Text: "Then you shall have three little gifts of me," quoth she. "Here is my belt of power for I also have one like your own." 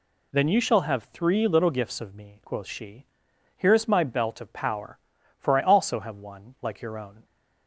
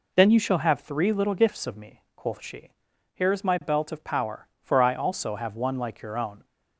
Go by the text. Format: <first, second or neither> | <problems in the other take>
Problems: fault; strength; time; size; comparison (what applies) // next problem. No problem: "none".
neither | none